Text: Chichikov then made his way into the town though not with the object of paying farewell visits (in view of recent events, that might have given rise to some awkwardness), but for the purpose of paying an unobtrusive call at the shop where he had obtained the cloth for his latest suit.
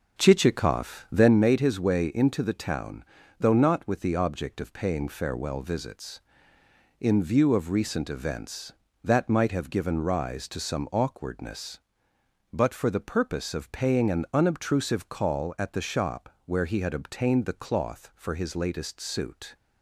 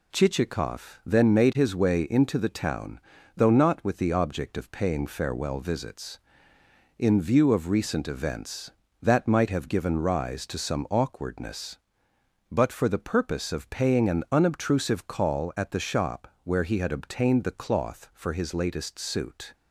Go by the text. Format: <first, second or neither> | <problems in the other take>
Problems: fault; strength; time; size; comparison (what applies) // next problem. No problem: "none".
second | starts louder than the rest; noticeable; until 1.5 s; 6 dB // pauses between "town" and "though"; slight; at 3.0 s; 0.34 s long; slight in the second